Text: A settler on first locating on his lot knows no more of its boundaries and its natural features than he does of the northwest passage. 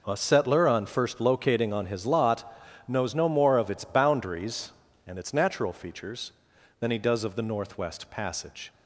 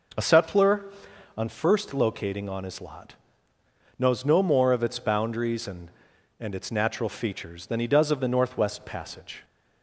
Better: first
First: pauses between "lot" and "knows"; slight; at 2.5 s; 0.34 s long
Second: pauses between "lot" and "knows"; noticeable; at 3.1 s; 0.84 s long // says "and" twice; at 6.3 s

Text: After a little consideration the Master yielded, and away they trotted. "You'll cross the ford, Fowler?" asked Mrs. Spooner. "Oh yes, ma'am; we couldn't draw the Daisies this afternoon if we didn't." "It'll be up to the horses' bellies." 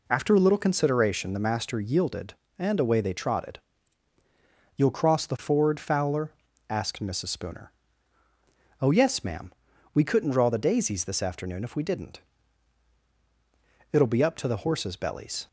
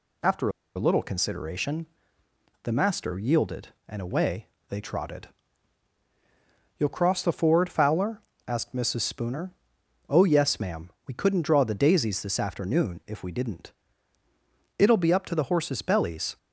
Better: first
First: none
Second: pauses between "After" and "a"; slight; at 0.4 s; 0.26 s long // pauses between "consideration" and "the"; noticeable; at 1.8 s; 0.78 s long // pauses between "away" and "they"; slight; at 4.4 s; 0.22 s long

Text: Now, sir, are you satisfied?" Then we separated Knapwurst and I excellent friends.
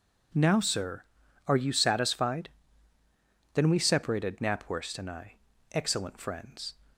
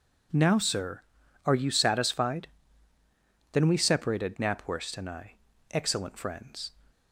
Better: neither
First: pauses between "I" and "excellent"; at 5.3 s; 0.38 s long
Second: pauses between "I" and "excellent"; at 5.3 s; 0.38 s long

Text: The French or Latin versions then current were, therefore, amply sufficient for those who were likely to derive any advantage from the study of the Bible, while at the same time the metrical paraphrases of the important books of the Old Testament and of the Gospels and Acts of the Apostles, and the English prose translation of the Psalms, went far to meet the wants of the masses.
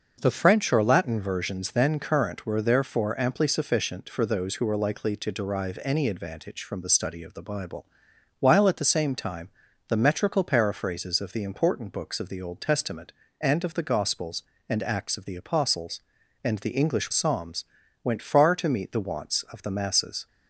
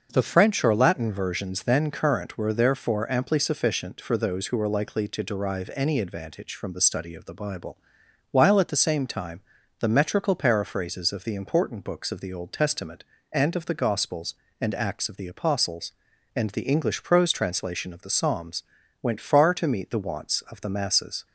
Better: second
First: starts louder than the rest; noticeable; until 1.2 s; 6 dB // pauses between "time" and "the"; at 9.4 s; 0.38 s long // skips "prose translation of the"; at 17.1 s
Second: starts louder than the rest; noticeable; until 1.1 s; 6 dB // pauses between "time" and "the"; at 9.4 s; 0.38 s long

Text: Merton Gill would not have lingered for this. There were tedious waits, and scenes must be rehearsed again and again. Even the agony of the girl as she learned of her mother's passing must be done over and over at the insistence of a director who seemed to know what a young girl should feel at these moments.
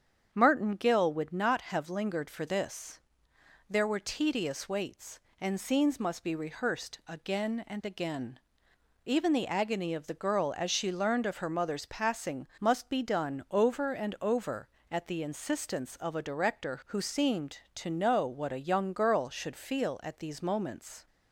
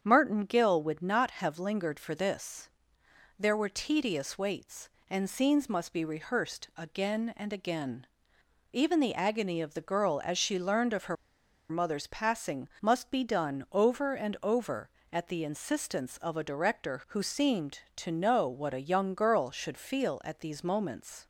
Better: first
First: starts louder than the rest; strong; until 1.3 s; 8 dB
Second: starts louder than the rest; strong; until 1.0 s; 7.5 dB // pauses between "her" and "mother's"; noticeable; at 11.1 s; 0.55 s long

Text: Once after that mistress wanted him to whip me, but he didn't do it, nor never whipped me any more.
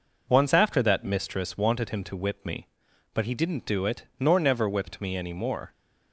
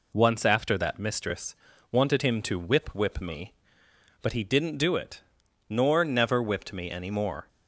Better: first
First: none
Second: pauses between "mistress" and "wanted"; slight; at 1.5 s; 0.34 s long // says "whip" twice; at 2.9 s

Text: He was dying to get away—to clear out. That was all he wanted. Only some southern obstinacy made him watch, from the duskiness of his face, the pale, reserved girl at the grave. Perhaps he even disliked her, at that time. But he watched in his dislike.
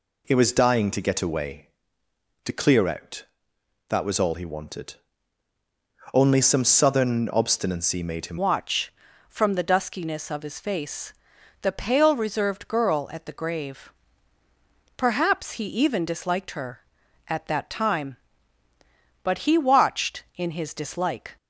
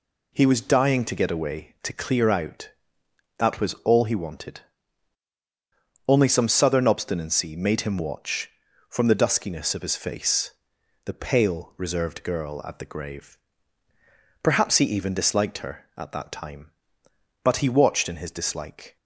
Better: second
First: changes voice at "watch"; from 8.3 s on; 13.0 s long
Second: none

